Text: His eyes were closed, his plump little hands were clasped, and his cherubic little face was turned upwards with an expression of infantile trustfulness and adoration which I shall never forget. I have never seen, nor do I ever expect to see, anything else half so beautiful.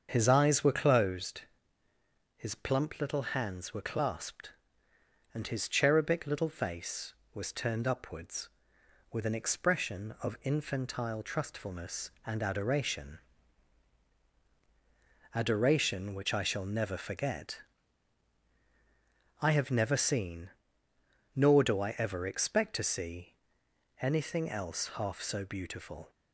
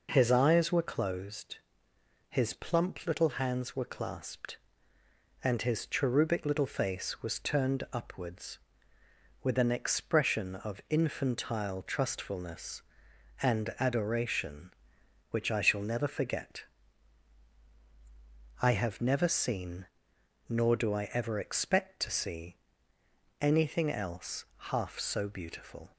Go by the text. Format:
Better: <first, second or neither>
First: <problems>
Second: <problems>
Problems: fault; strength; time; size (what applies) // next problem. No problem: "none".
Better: second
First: starts louder than the rest; until 1.1 s; 7 dB // says "adoration" twice; at 15.3 s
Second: none